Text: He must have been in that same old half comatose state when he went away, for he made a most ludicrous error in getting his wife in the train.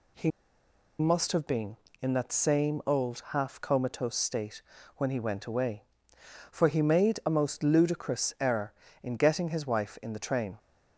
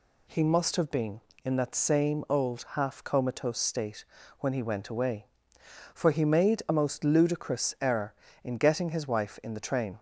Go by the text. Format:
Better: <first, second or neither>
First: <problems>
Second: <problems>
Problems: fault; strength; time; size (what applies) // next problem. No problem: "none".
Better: second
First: pauses between "He" and "must"; noticeable; at 0.2 s; 0.69 s long // pauses between "state" and "when"; at 4.6 s; 0.38 s long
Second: pauses between "state" and "when"; at 4.0 s; 0.38 s long